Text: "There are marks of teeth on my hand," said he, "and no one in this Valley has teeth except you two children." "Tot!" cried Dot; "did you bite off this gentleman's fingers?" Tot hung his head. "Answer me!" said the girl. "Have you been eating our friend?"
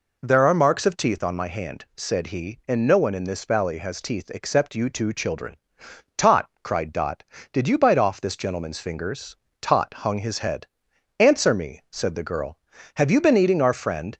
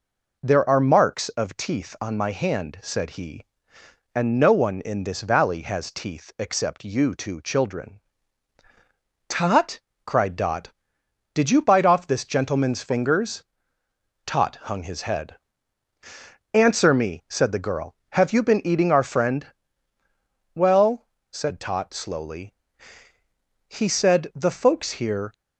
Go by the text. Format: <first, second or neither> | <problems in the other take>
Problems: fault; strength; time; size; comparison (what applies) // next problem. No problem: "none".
first | goes on to say "Well said Tot slowly he said the folks here"; strong; from 20.5 s on; 4.7 s long